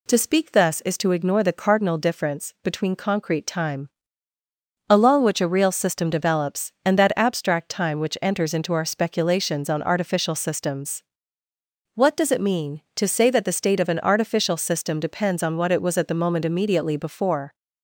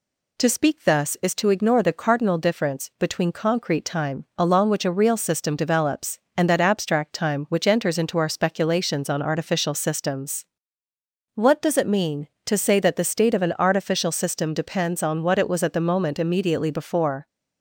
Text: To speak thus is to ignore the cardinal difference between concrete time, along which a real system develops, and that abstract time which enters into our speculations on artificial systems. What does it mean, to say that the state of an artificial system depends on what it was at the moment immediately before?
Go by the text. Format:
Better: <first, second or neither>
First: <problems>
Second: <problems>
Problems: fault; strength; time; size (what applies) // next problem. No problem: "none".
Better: neither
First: none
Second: none